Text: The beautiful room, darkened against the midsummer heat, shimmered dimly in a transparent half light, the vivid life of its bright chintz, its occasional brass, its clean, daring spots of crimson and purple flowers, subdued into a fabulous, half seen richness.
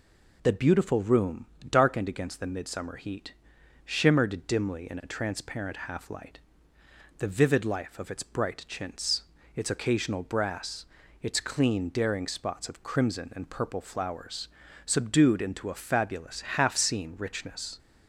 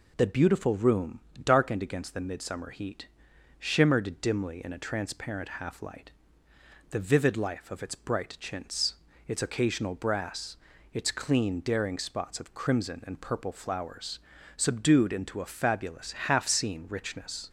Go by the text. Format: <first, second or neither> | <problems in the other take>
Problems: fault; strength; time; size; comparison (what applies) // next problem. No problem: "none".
neither | none